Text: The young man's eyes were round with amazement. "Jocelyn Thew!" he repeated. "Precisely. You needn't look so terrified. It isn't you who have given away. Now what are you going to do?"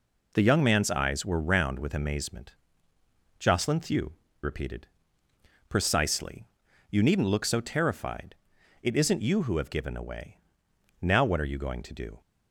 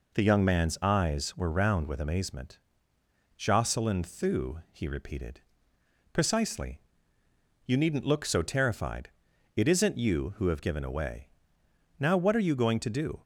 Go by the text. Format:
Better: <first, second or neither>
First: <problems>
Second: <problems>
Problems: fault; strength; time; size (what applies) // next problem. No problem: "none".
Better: second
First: skips "he"; at 4.2 s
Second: none